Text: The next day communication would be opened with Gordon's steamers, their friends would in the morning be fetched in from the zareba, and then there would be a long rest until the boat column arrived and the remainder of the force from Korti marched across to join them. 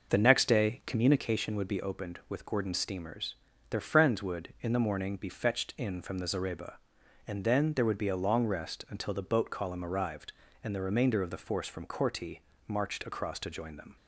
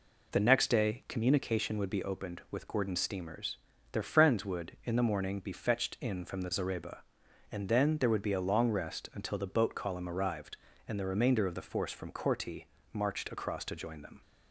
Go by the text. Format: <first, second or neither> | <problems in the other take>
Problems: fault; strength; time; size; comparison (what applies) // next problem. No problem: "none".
second | starts louder than the rest; noticeable; until 1.3 s; 6 dB // pauses between "Korti" and "marched"; slight; at 12.4 s; 0.26 s long; slight in the second